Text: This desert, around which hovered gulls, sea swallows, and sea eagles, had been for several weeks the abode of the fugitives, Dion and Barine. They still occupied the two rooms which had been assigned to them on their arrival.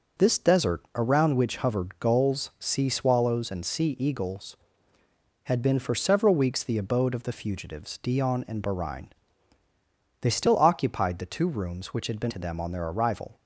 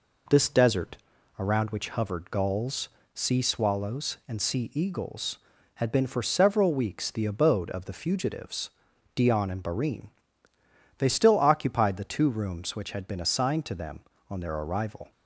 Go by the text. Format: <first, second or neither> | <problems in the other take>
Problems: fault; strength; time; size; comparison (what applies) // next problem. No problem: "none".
second | skips "assigned"; at 12.3 s